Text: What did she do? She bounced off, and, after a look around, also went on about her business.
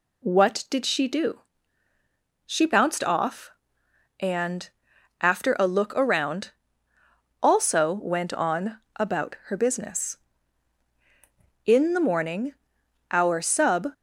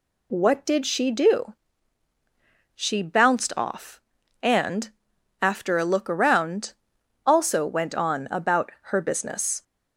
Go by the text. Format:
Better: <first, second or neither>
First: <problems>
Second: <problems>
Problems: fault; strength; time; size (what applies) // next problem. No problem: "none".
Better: second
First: pauses between "on" and "about"; slight; at 8.7 s; 0.18 s long // goes on to say "In the morning our sub"; strong; from 11.6 s on; 2.2 s long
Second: none